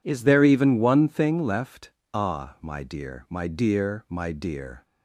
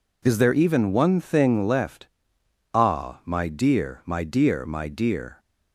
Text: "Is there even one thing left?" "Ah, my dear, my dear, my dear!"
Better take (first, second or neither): neither